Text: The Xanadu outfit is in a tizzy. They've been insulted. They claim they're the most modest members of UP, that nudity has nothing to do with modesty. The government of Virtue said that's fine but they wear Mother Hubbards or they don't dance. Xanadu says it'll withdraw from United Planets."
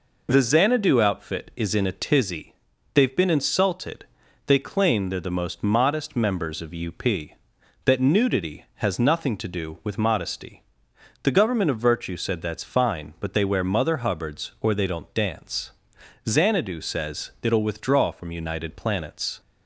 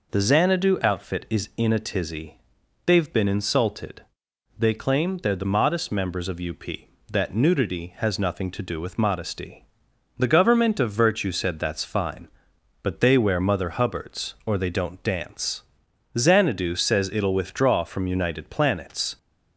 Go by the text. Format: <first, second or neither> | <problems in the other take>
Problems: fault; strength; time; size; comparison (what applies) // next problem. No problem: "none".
first | skips "most"; at 5.4 s